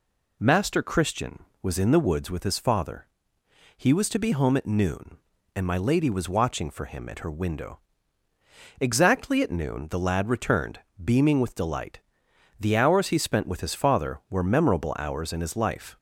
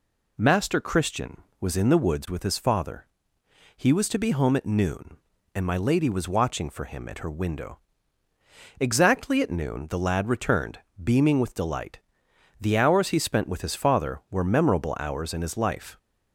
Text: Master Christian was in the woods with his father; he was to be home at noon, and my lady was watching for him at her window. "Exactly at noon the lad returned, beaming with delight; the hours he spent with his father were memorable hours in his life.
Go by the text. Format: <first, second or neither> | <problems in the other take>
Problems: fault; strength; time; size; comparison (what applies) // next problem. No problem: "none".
neither | none